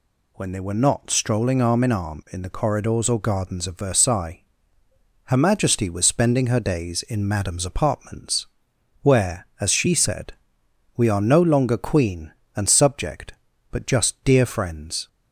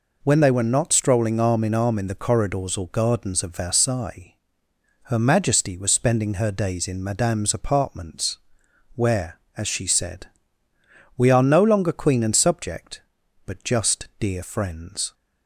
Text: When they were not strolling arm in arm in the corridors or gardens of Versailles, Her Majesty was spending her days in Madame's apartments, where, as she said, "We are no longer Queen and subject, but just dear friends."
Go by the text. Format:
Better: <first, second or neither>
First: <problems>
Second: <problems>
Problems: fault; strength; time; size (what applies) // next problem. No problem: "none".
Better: neither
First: none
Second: none